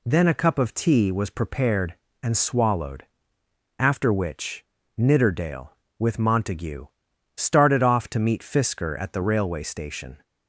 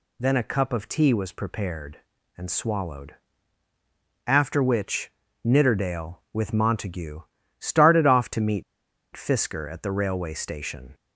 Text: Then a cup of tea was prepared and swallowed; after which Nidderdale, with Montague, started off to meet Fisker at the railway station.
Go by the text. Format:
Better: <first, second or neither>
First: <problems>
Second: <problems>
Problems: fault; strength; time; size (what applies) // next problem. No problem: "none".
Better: first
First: pauses between "which" and "Nidderdale"; slight; at 4.6 s; 0.32 s long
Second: pauses between "which" and "Nidderdale"; slight; at 5.1 s; 0.32 s long // pauses between "meet" and "Fisker"; noticeable; at 8.6 s; 0.51 s long